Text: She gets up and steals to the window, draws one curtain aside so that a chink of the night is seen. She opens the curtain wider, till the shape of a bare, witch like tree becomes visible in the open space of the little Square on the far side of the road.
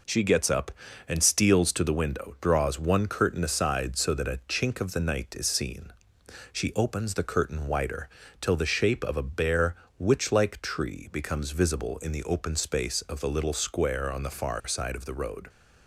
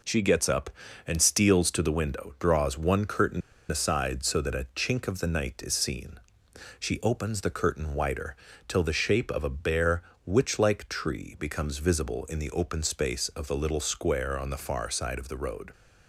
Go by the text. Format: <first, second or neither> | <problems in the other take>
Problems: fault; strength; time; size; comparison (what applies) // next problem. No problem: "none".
first | pauses between "curtain" and "aside"; slight; at 3.4 s; 0.28 s long